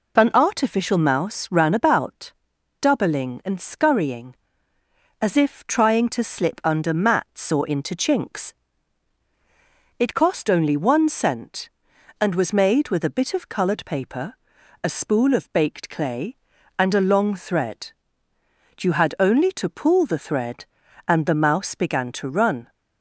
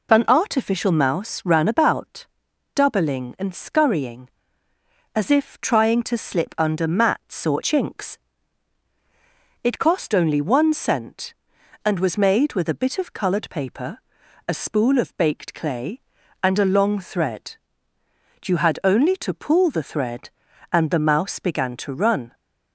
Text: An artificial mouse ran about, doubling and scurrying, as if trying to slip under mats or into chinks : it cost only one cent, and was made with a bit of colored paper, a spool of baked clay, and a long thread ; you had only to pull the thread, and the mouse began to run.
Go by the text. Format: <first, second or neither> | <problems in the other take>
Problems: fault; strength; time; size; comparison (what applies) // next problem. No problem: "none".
first | skips "into"; at 7.6 s